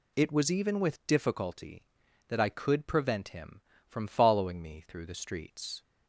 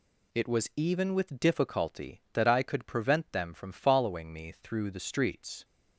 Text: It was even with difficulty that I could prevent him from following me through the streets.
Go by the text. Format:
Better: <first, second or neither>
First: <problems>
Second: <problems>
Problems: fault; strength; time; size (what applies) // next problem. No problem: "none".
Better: first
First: none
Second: says "them" for "him"; at 3.3 s